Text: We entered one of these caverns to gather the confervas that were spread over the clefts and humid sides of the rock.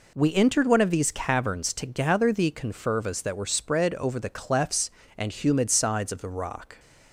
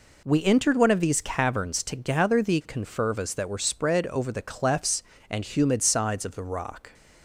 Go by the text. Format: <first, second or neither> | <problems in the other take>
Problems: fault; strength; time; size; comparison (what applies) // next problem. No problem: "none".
neither | none